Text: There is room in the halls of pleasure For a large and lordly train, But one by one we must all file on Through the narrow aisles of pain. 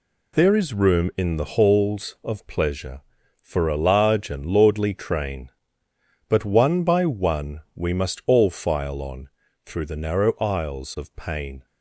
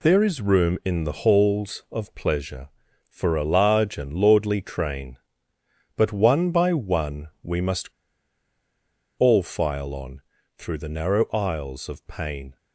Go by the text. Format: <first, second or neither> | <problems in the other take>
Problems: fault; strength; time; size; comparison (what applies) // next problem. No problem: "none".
first | pauses between "one" and "we"; slight; at 7.2 s; 0.16 s long; slight in the first // pauses between "must" and "all"; strong; at 7.8 s; 1.3 s long // pauses between "on" and "Through"; slight; at 10.2 s; 0.36 s long; slight in the first